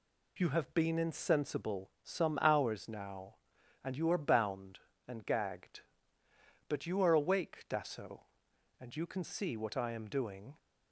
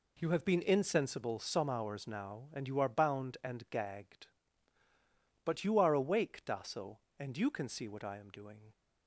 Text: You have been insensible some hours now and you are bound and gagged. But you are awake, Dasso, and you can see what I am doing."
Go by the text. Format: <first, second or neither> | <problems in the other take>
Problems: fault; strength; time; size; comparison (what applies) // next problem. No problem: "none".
neither | none